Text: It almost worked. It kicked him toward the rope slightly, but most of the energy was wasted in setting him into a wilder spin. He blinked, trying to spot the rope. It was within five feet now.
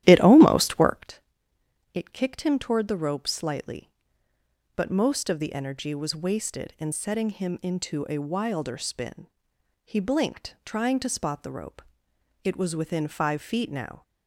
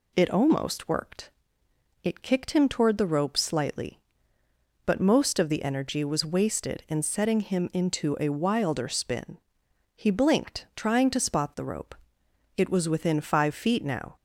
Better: second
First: starts louder than the rest; strong; until 1.1 s; 12.5 dB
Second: none

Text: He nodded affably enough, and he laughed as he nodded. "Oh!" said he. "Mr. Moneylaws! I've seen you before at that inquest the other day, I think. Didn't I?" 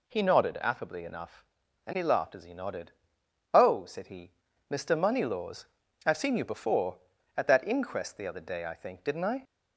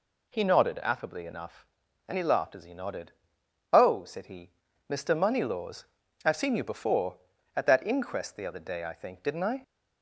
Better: neither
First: none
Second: none

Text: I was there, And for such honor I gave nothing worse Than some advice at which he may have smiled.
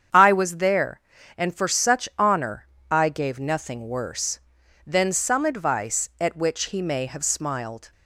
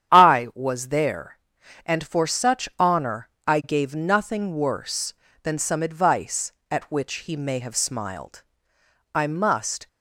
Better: first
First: starts louder than the rest; strong; until 1.4 s; 8 dB // pauses between "honor" and "I"; slight; at 2.6 s; 0.24 s long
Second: starts louder than the rest; strong; until 1.1 s; 9.5 dB // pauses between "honor" and "I"; slight; at 3.2 s; 0.20 s long // goes on to say "I must"; noticeable; from 9.1 s on; 0.74 s long

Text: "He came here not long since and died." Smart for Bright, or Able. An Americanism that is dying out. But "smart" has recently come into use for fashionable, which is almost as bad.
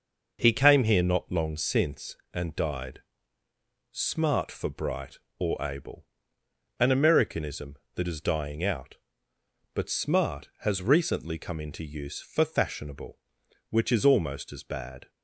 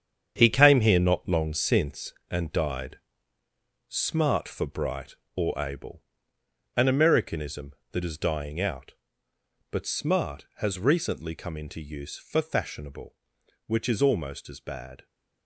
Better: first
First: none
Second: gets quieter; strong; throughout; 9.5 dB

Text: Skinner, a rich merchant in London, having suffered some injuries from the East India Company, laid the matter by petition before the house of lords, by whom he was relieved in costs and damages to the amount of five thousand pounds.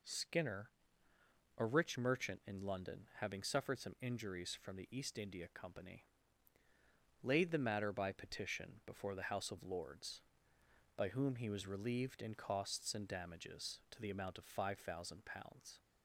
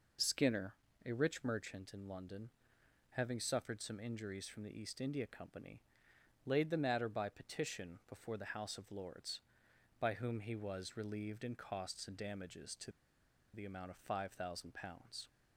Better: first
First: none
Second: pauses between "to" and "the"; noticeable; at 12.9 s; 0.62 s long

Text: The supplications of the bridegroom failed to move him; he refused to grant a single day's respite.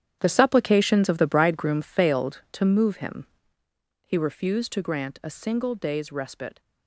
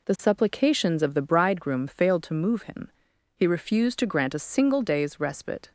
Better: second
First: gets quieter; strong; throughout; 13.5 dB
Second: none

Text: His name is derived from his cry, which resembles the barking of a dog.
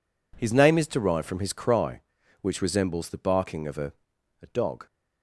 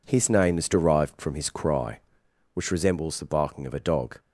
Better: second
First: says "a" twice; at 4.4 s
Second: none

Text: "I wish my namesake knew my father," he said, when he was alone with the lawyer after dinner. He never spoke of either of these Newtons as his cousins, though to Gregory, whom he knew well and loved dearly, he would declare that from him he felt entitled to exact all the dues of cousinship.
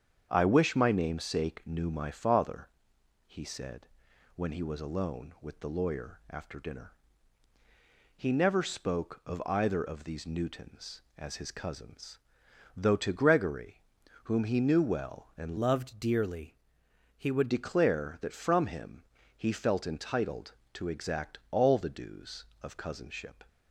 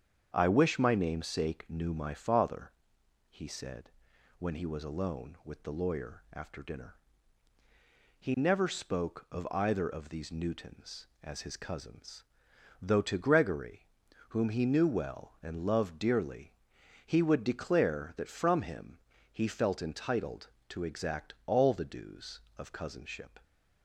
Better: second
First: starts louder than the rest; strong; until 1.3 s; 7.5 dB // changes voice from "loved" to "would"; from 15.5 to 17.4 s; 1.9 s long // pauses between "him" and "he"; slight; at 19.0 s; 0.32 s long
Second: starts louder than the rest; strong; until 1.3 s; 7.5 dB // pauses between "him" and "he"; slight; at 18.9 s; 0.32 s long

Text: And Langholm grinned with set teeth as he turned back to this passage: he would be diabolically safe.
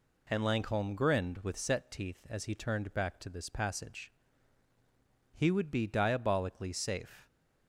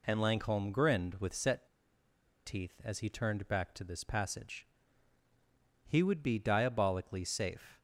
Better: first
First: none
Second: pauses between "set" and "teeth"; noticeable; at 1.6 s; 0.79 s long

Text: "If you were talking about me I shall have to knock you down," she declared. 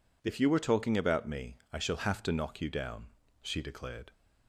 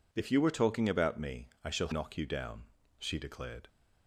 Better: first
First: pauses between "me" and "I"; slight; at 1.5 s; 0.16 s long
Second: pauses between "me" and "I"; slight; at 1.4 s; 0.16 s long // skips "have to"; at 1.9 s

